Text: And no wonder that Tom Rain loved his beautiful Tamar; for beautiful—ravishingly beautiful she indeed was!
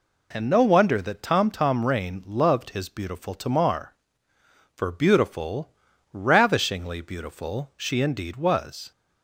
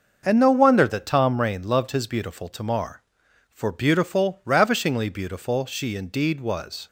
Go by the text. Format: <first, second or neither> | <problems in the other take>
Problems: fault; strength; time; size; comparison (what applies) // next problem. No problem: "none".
second | says "Tom" twice; at 1.5 s